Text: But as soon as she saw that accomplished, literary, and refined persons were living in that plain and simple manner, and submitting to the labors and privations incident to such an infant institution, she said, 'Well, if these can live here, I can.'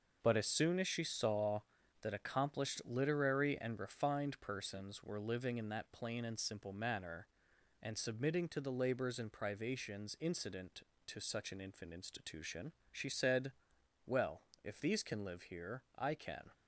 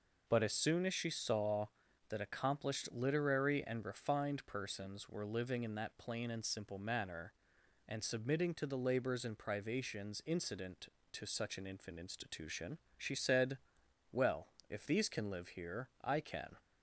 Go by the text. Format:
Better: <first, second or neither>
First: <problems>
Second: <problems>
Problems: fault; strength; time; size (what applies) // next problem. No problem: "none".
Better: second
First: gets quieter; strong; throughout; 8.5 dB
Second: none